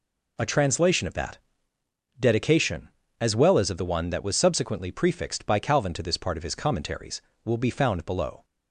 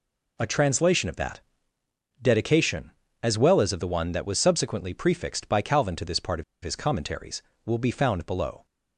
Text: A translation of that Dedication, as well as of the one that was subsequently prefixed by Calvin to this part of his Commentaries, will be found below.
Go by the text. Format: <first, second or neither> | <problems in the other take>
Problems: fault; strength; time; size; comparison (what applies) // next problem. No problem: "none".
first | pauses between "that" and "Dedication"; noticeable; at 1.4 s; 0.80 s long; noticeable in the first // pauses between "of" and "his"; slight; at 6.4 s; 0.19 s long